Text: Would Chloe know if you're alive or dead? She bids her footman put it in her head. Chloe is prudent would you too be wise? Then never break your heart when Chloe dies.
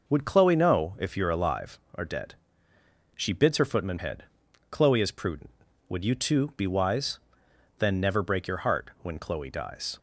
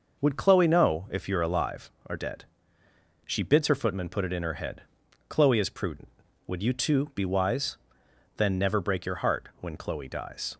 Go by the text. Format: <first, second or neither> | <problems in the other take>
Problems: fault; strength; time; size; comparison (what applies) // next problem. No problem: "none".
second | skips "put it in her"; at 3.9 s